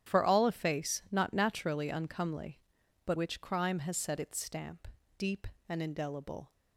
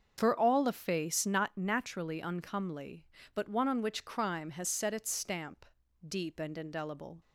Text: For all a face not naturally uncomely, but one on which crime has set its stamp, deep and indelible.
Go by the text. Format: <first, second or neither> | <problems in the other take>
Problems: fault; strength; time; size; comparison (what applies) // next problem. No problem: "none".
second | starts louder than the rest; strong; until 1.1 s; 10 dB; also in the second // skips "one on"; at 3.1 s